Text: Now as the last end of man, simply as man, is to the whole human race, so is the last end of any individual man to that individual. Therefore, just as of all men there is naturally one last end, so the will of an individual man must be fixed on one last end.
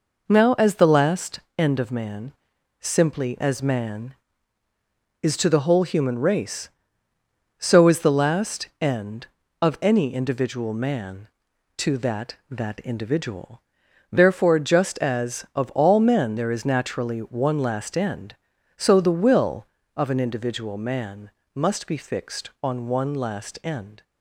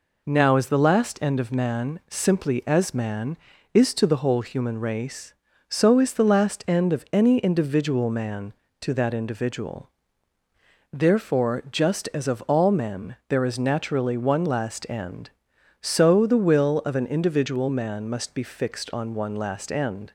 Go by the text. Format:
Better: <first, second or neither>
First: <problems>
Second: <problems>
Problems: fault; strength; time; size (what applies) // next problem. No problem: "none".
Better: second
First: pauses between "last" and "end"; slight; at 1.3 s; 0.18 s long // pauses between "last" and "end"; slight; at 8.6 s; 0.16 s long // says "that" twice; at 12.4 s // pauses between "man" and "must"; slight; at 21.3 s; 0.22 s long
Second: none